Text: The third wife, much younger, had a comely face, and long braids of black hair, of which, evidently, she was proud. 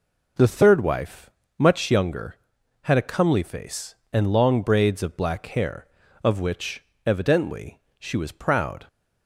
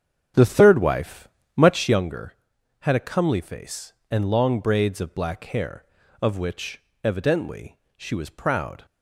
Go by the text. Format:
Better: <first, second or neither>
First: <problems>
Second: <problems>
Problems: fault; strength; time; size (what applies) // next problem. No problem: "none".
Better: first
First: none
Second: starts louder than the rest; strong; until 2.1 s; 7.5 dB